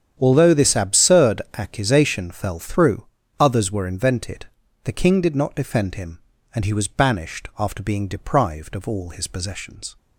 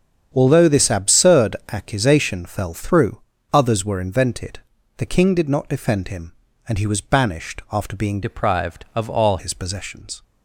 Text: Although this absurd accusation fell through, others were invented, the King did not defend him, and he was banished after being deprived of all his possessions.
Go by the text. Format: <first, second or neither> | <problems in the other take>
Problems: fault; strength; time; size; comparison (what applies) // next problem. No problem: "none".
first | starts louder than the rest; strong; until 1.3 s; 8 dB; strong in the first // pauses between "absurd" and "accusation"; slight; at 1.5 s; 0.16 s long; slight in the first // changes voice from "deprived" to "all"; from 8.2 to 9.3 s; 1.1 s long